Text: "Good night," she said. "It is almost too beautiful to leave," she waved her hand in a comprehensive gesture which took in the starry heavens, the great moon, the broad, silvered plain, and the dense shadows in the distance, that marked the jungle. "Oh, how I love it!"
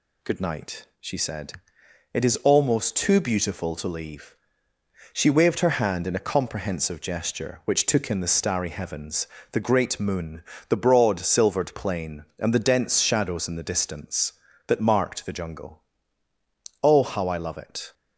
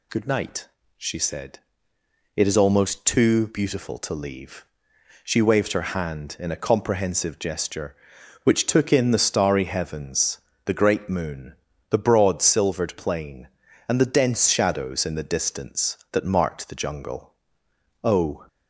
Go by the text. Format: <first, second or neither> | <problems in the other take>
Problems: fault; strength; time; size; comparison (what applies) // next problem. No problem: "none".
first | stops before "how I love it"; at 18.4 s